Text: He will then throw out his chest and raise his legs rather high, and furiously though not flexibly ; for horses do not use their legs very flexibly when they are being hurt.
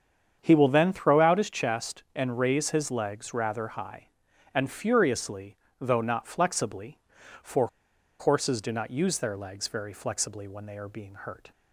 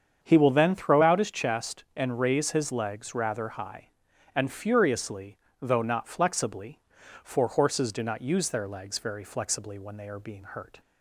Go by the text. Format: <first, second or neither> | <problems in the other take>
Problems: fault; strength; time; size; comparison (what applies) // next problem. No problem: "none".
second | starts louder than the rest; strong; until 1.4 s; 7.5 dB; strong in the second // pauses between "furiously" and "though"; slight; at 5.5 s; 0.24 s long; slight in the second // pauses between "for" and "horses"; noticeable; at 7.6 s; 0.52 s long